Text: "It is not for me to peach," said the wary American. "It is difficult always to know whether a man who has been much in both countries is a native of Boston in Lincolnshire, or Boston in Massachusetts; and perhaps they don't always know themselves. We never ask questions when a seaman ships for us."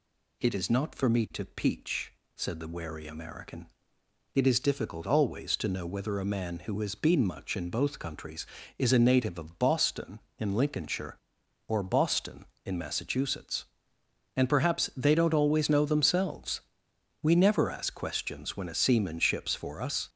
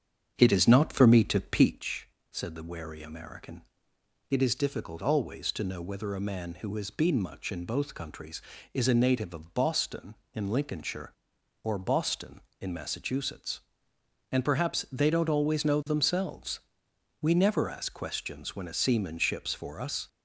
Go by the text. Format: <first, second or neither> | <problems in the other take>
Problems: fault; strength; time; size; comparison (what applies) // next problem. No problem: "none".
first | starts louder than the rest; strong; until 1.9 s; 8 dB